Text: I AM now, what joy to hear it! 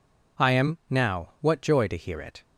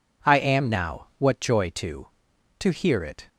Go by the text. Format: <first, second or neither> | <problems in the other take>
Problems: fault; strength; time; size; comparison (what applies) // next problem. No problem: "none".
first | says "to" twice; at 2.5 s